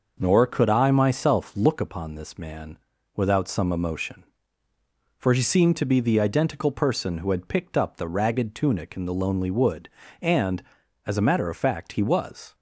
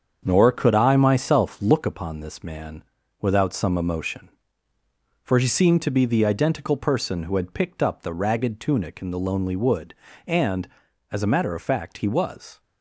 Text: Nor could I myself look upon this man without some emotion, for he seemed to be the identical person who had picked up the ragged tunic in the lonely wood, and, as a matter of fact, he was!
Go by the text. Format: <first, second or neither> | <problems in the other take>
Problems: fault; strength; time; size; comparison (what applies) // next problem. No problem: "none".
first | gets quieter; throughout; 6.5 dB // starts louder than the rest; strong; until 1.2 s; 7 dB; noticeable in the first // pauses between "man" and "without"; at 2.8 s; 0.38 s long; also in the first